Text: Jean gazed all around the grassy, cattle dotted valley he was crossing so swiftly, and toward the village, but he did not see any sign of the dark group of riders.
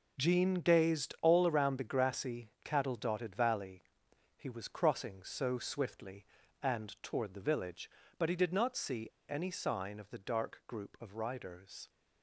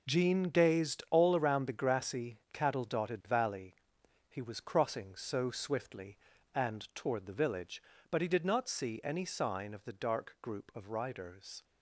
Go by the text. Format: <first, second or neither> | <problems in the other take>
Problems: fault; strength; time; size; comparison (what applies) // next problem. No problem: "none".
second | pauses between "valley" and "he"; noticeable; at 3.8 s; 0.56 s long; noticeable in the second // pauses between "see" and "any"; slight; at 9.0 s; 0.21 s long